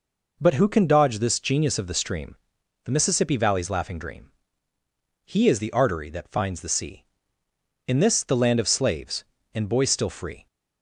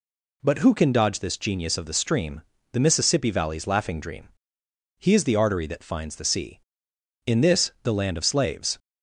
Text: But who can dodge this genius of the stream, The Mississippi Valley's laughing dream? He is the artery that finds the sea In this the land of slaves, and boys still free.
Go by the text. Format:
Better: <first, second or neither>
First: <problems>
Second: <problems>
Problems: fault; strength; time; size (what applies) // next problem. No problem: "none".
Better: first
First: none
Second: stops before "and boys still free"; at 8.7 s